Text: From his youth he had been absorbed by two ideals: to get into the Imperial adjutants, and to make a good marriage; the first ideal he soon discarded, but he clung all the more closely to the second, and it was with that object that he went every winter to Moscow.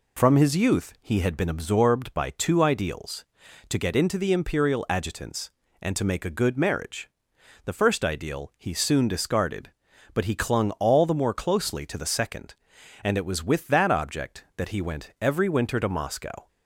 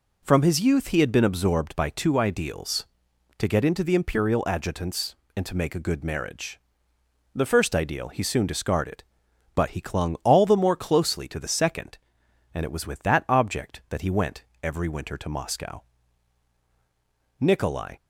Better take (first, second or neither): first